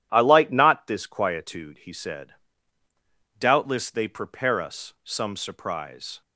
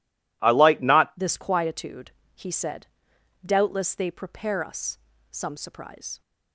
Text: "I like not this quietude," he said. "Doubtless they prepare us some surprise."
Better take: first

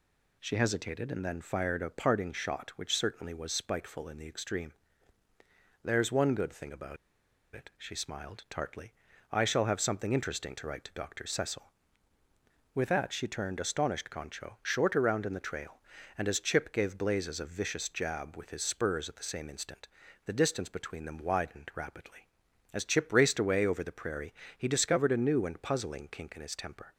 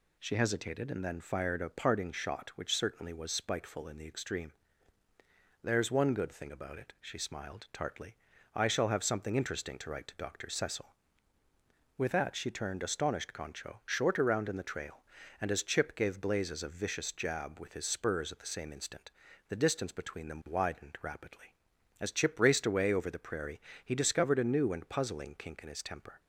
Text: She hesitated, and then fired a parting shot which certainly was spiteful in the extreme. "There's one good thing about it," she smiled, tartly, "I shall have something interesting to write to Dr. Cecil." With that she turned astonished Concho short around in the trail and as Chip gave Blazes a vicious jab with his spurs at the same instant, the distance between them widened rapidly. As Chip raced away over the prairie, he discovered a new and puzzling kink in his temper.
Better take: second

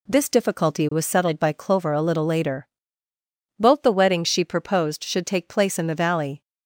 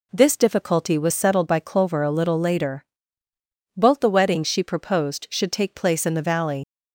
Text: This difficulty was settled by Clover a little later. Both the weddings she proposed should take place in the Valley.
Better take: first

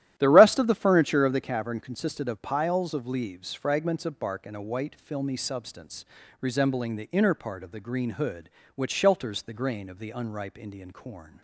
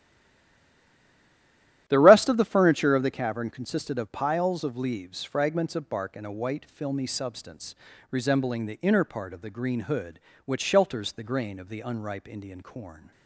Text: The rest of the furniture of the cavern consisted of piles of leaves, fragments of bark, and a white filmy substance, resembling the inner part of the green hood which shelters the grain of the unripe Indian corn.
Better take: first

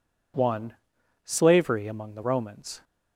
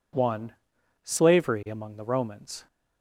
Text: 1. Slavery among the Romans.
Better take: neither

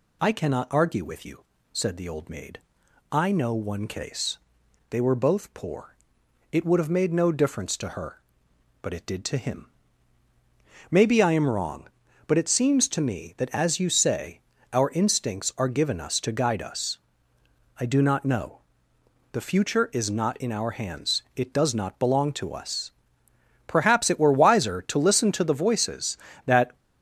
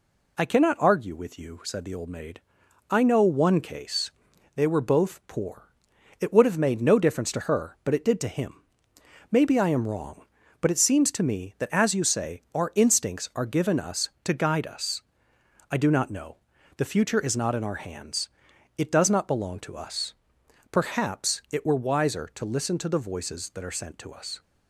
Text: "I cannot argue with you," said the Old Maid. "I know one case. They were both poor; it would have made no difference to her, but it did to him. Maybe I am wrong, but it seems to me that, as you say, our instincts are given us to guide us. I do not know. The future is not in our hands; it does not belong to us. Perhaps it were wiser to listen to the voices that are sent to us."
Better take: second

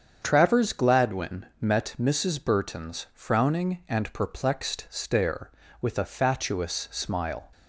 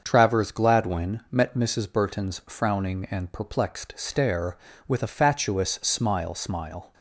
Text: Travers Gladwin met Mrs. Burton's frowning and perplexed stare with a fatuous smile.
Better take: first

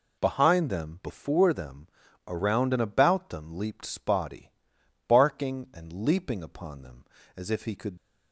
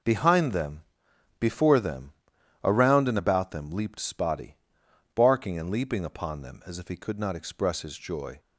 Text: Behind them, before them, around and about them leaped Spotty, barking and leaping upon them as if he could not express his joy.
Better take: second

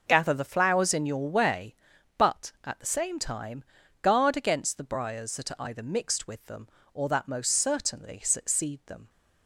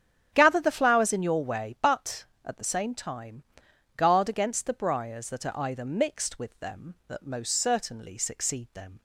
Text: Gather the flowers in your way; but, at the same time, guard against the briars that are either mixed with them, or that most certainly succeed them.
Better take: first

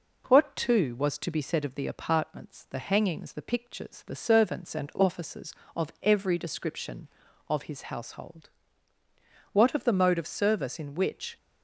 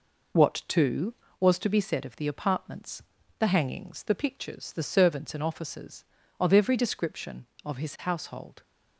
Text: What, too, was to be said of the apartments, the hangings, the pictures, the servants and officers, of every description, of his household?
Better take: second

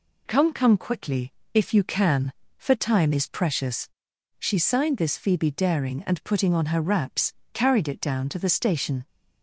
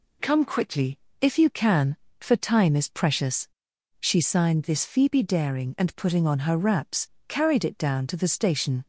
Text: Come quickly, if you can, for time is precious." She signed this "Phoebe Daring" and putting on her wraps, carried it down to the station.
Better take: second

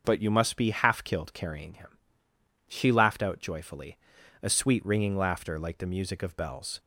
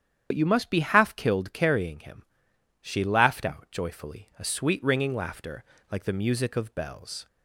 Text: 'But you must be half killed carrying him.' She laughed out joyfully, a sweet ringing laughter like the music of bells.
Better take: first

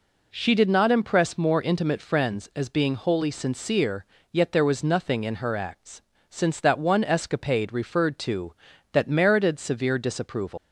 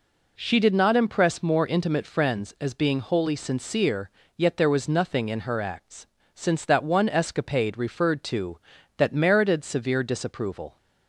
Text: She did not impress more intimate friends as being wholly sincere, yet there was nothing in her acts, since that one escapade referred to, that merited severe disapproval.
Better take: second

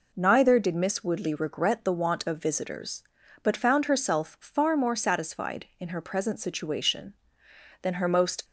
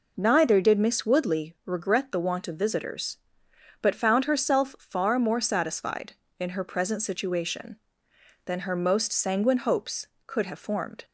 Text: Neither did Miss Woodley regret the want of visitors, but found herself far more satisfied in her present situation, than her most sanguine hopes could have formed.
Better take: second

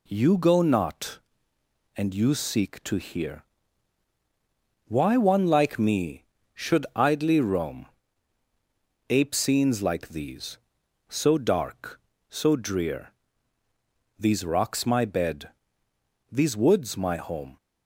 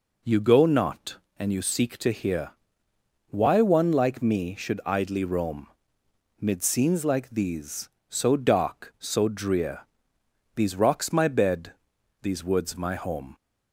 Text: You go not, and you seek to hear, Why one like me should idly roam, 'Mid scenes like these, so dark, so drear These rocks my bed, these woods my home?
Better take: second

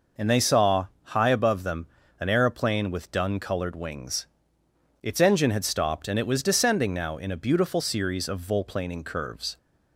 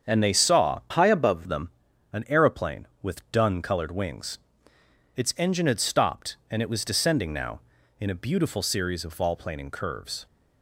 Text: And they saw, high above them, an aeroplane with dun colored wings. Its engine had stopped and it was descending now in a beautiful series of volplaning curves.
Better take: first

